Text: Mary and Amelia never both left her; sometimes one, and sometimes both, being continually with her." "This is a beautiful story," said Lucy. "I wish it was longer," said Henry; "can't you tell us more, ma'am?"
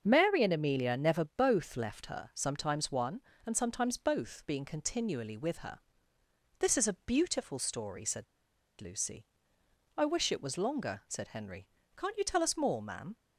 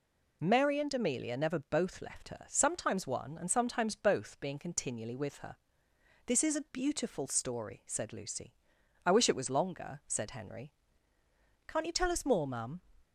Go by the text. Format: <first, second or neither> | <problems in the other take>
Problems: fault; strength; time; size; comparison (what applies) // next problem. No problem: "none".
second | starts louder than the rest; until 1.0 s; 6.5 dB // pauses between "said" and "Lucy"; noticeable; at 8.2 s; 0.56 s long